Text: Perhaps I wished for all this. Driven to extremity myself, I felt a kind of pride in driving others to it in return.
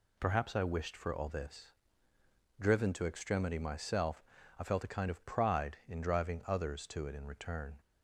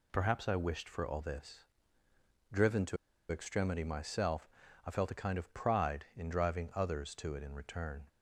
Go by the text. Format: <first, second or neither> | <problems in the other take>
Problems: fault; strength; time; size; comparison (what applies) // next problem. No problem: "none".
first | pauses between "to" and "extremity"; slight; at 2.9 s; 0.34 s long